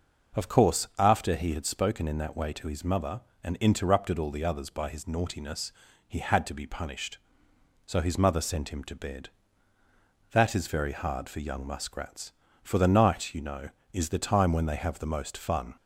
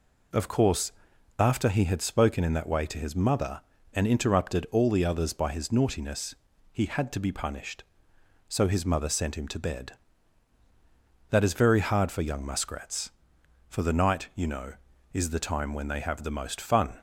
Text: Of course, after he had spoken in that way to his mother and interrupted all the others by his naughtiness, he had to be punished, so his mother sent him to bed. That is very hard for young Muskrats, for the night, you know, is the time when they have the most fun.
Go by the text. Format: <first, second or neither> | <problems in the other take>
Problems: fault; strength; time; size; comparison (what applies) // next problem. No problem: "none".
neither | none